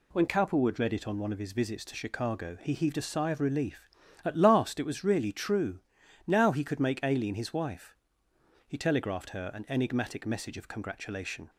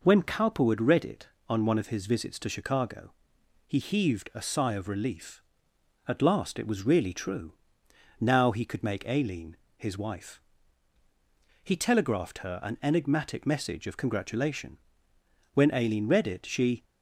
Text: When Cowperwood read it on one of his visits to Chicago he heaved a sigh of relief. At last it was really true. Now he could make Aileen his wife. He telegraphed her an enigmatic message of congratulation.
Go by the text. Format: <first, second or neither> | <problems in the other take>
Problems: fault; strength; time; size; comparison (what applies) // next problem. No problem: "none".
first | pauses between "Chicago" and "he"; noticeable; at 3.1 s; 0.56 s long // pauses between "Aileen" and "his"; slight; at 9.5 s; 0.22 s long // goes on to say "When Aileen read it she"; noticeable; from 15.5 s on; 1.3 s long